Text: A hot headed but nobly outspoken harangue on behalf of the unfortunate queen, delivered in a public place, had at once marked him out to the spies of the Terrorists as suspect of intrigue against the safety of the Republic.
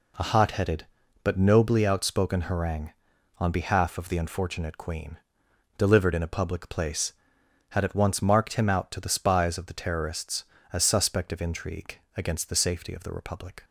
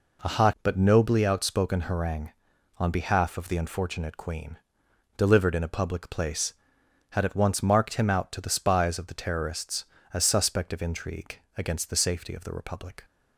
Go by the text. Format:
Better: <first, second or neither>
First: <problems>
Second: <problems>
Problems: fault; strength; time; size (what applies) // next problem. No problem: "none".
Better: first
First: pauses between "intrigue" and "against"; slight; at 11.9 s; 0.18 s long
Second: skips "headed"; at 0.5 s // pauses between "intrigue" and "against"; slight; at 11.3 s; 0.18 s long